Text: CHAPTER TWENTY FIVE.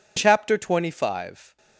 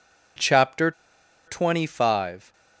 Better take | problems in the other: first | pauses between "CHAPTER" and "TWENTY"; noticeable; at 0.9 s; 0.55 s long

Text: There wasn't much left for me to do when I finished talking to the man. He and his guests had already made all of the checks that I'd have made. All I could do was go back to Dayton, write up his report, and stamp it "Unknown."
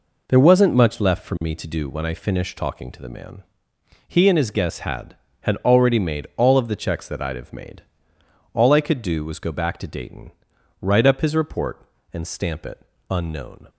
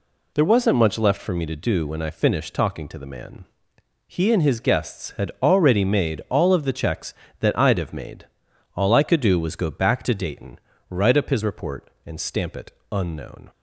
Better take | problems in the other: second | says "had" twice; at 5.4 s // pauses between "it" and "Unknown"; slight; at 12.8 s; 0.28 s long; slight in the second

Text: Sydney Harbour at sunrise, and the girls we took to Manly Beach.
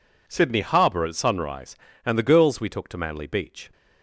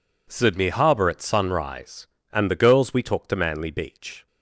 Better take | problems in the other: neither | none

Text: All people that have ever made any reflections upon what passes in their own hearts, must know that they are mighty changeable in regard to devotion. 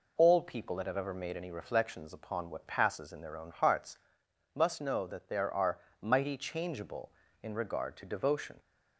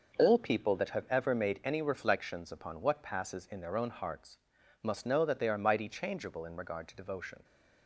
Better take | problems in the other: second | says "there" for "they"; at 5.2 s // pauses between "are" and "mighty"; slight; at 5.7 s; 0.22 s long

